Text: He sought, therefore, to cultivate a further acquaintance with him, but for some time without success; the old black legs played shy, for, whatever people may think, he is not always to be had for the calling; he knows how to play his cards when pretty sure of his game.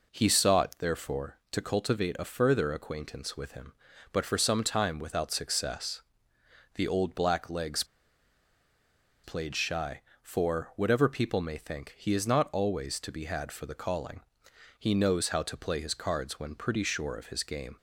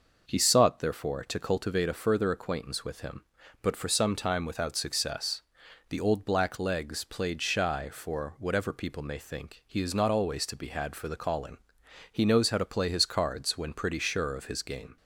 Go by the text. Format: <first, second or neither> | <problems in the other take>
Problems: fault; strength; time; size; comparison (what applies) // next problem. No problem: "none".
second | pauses between "legs" and "played"; strong; at 7.8 s; 1.4 s long